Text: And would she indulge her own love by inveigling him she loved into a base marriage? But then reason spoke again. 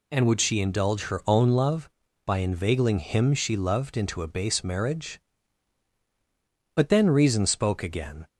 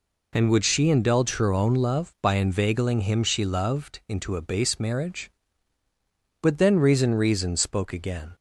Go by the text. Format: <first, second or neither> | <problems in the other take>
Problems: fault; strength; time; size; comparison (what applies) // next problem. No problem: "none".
first | says "reason" twice; at 7.1 s